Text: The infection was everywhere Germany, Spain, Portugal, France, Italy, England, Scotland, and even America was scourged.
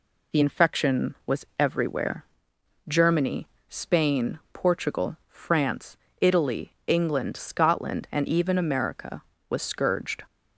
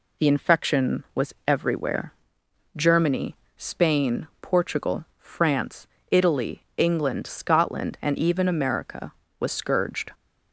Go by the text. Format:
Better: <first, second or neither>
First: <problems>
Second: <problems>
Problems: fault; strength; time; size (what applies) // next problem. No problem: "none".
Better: neither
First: pauses between "everywhere" and "Germany"; noticeable; at 2.2 s; 0.64 s long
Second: pauses between "everywhere" and "Germany"; noticeable; at 2.1 s; 0.64 s long